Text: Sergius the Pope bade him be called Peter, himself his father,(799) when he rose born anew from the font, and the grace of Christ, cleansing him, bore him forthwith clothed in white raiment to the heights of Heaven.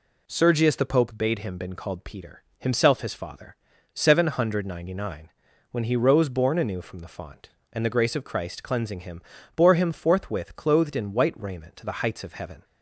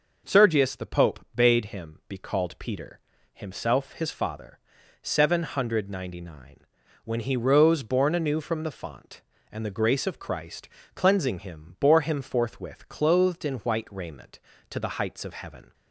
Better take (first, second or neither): second